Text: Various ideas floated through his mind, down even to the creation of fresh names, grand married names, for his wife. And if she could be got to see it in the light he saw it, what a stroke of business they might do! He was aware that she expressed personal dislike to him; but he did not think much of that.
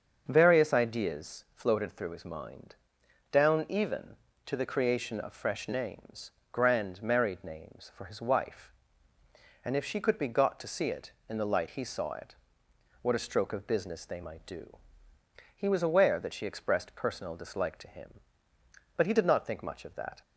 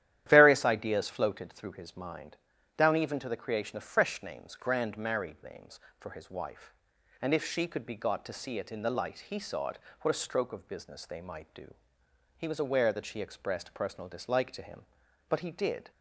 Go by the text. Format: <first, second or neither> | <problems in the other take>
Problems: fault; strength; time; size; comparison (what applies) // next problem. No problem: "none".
first | starts louder than the rest; strong; until 1.2 s; 12 dB; also in the first // stops before "not think much of that"; at 15.9 s